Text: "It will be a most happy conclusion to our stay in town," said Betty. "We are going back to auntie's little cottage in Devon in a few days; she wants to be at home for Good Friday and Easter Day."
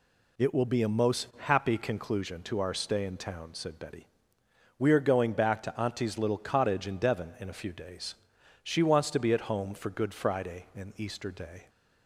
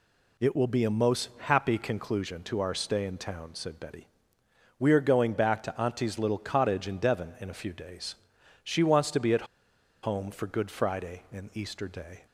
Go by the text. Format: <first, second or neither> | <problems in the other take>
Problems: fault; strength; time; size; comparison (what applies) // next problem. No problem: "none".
first | pauses between "at" and "home"; noticeable; at 9.4 s; 0.59 s long